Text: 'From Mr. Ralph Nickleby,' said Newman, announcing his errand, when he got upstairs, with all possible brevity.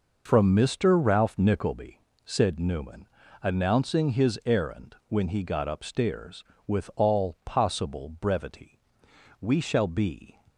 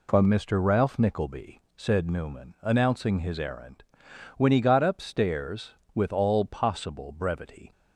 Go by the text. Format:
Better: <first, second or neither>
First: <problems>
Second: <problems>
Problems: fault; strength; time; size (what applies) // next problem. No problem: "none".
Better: second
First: goes on to say "We shall be"; noticeable; from 9.4 s on; 1.0 s long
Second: none